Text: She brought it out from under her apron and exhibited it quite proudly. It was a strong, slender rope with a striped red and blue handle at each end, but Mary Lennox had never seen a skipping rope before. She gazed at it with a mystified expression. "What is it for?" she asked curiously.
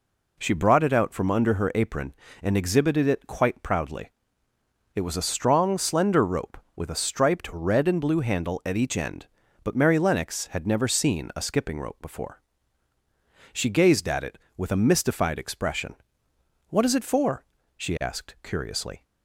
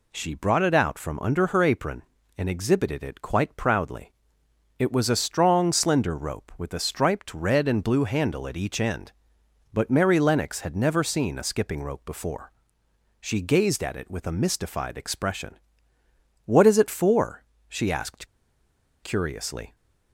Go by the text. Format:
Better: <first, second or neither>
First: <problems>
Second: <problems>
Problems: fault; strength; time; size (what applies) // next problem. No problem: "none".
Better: first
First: none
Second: pauses between "asked" and "curiously"; noticeable; at 18.2 s; 0.76 s long